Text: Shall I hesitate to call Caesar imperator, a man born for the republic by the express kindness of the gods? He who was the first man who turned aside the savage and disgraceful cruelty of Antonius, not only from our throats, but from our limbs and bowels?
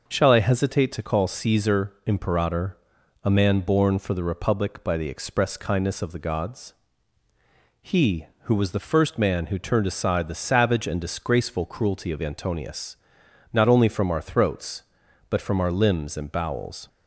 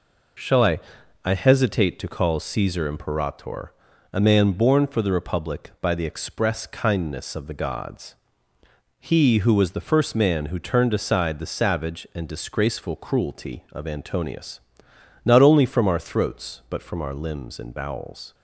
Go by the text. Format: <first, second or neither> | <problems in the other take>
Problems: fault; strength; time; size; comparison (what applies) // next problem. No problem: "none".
first | says "I" twice; at 1.2 s